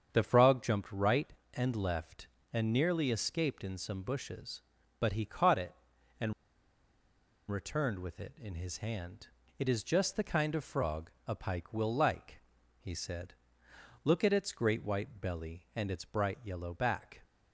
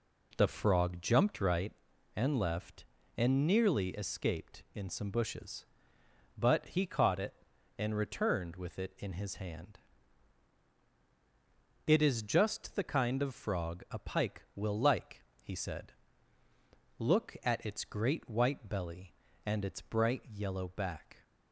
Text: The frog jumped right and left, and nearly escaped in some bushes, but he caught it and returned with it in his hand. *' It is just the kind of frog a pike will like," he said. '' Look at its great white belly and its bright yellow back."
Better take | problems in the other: second | starts louder than the rest; strong; until 1.1 s; 7.5 dB // pauses between "and" and "returned"; at 6.3 s; 1.1 s long // pauses between "frog" and "a"; slight; at 11.0 s; 0.16 s long

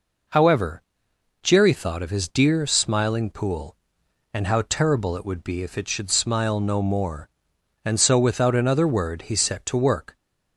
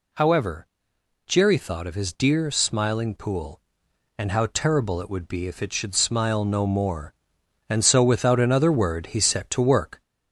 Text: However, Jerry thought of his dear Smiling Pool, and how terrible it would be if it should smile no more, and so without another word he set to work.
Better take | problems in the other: first | gets louder; slight; throughout; 2 dB

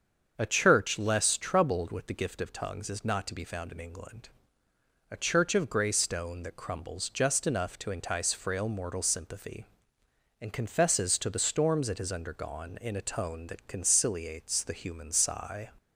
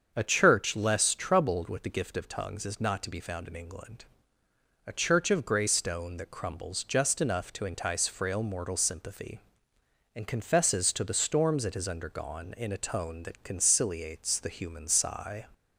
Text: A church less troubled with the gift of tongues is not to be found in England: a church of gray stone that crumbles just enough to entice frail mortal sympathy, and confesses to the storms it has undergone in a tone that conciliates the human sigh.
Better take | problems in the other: neither | starts louder than the rest; the same in both

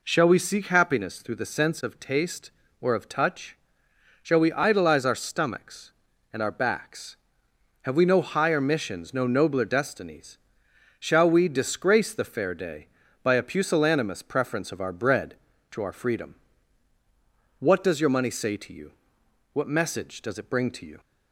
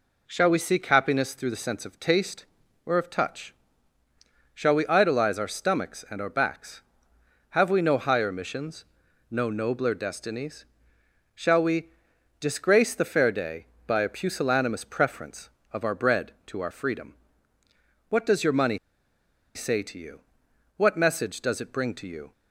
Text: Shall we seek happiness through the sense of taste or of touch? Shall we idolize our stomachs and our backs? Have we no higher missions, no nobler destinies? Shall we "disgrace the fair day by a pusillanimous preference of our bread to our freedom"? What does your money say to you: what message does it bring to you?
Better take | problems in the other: first | pauses between "we" and "disgrace"; noticeable; at 11.9 s; 0.50 s long // pauses between "money" and "say"; noticeable; at 18.7 s; 0.77 s long

